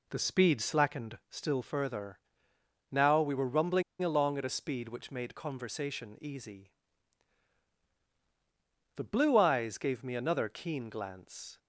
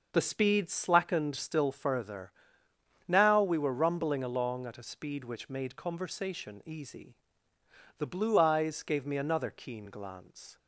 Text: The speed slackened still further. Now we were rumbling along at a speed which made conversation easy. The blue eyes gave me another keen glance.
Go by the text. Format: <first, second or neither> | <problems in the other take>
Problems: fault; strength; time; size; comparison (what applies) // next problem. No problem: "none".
second | pauses between "rumbling" and "along"; slight; at 3.8 s; 0.19 s long